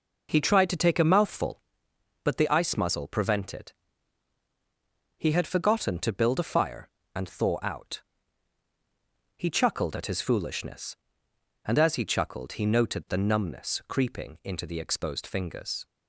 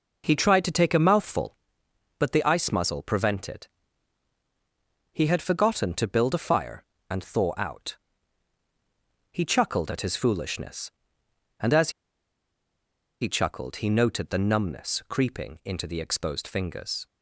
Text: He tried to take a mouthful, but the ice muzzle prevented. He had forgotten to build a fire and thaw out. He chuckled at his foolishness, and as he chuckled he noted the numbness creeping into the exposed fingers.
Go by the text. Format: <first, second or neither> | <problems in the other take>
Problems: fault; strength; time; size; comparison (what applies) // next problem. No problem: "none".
first | pauses between "as" and "he"; strong; at 11.9 s; 1.3 s long